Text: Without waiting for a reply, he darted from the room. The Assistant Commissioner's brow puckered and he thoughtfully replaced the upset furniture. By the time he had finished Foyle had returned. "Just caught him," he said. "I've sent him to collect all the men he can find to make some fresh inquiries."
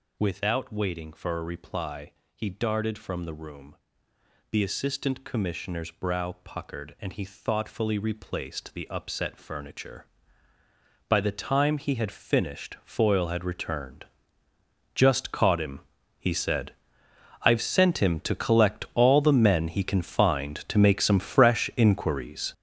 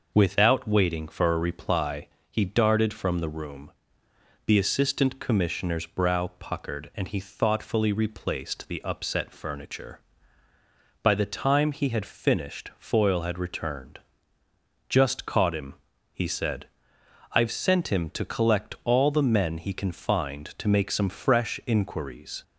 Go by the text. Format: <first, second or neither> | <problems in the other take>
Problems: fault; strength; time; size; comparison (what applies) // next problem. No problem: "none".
second | gets louder; strong; throughout; 10 dB